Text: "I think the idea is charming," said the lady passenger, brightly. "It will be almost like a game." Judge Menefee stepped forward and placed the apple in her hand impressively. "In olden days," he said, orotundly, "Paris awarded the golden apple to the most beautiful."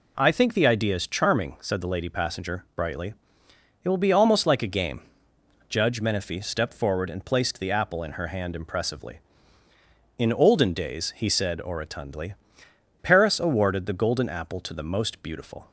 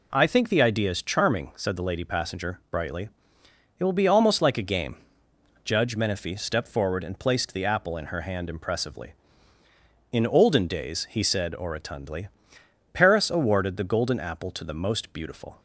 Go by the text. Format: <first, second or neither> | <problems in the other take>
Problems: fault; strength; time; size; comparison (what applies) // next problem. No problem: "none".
neither | none